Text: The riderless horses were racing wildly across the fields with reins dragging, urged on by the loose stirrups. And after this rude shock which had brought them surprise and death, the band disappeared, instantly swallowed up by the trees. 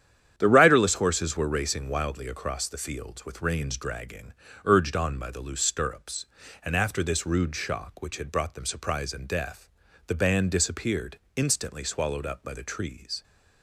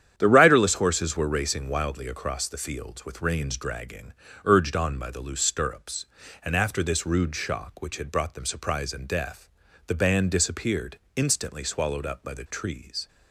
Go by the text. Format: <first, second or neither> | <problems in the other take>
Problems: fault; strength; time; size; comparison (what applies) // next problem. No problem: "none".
neither | starts louder than the rest; strong; the same in both